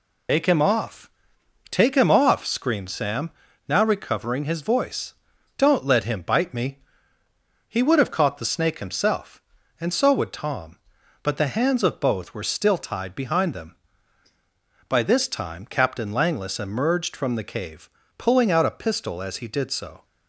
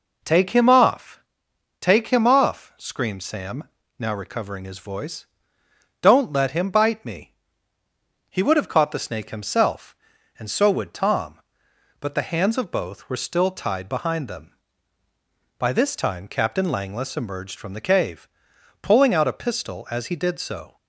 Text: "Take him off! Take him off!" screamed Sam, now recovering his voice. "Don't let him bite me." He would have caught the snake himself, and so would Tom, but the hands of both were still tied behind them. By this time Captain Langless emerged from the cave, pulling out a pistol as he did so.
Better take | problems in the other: second | loses the start of "Take"; at 0.2 s; 80 ms

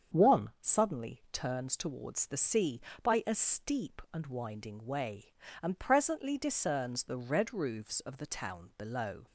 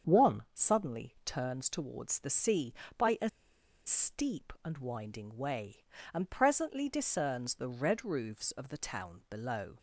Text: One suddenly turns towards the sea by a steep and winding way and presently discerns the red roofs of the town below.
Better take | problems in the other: first | starts louder than the rest; strong; until 1.1 s; 7 dB; strong in the first // pauses between "a" and "steep"; noticeable; at 3.2 s; 0.57 s long

